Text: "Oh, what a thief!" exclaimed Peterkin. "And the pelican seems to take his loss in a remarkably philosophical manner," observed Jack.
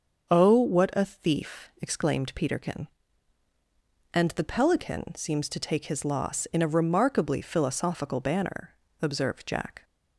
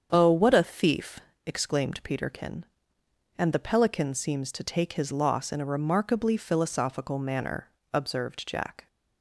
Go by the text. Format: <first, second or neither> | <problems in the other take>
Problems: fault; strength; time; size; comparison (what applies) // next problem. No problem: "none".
second | starts louder than the rest; until 1.3 s; 7 dB; strong in the second // says "banner" for "manner"; at 8.2 s